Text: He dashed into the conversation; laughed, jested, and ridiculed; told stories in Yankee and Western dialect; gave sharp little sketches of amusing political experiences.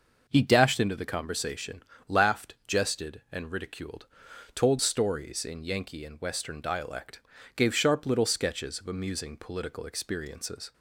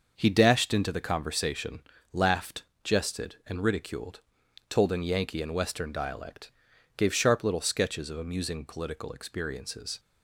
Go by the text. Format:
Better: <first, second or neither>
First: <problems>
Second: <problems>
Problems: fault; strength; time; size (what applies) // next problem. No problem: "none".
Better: first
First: none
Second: starts louder than the rest; until 1.1 s; 6 dB // skips "stories"; at 4.9 s